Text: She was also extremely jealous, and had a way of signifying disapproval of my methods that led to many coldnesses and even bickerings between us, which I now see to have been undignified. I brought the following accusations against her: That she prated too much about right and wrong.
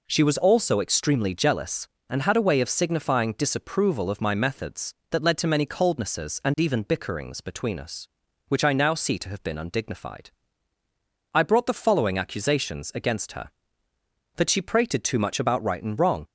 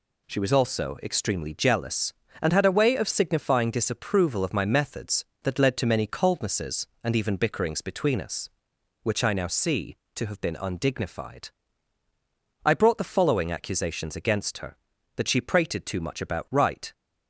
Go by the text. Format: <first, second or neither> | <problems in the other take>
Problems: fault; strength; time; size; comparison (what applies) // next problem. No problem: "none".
first | stops before "and wrong"; at 16.9 s